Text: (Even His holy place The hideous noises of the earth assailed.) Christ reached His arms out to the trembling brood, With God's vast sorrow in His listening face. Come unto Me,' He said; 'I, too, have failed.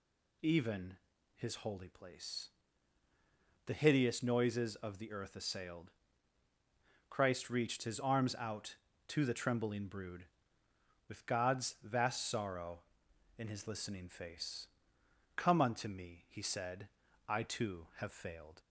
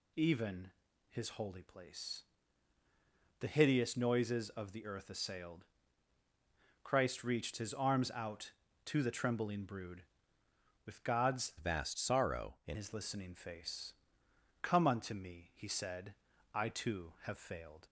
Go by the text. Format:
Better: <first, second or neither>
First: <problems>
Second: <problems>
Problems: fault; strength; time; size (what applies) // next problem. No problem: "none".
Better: first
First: pauses between "Even" and "His"; at 0.9 s; 0.40 s long // pauses between "place" and "The"; at 2.4 s; 1.1 s long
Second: pauses between "Even" and "His"; at 0.6 s; 0.40 s long // pauses between "place" and "The"; at 2.2 s; 1.1 s long // changes voice from "vast" to "in"; from 11.5 to 12.7 s; 1.2 s long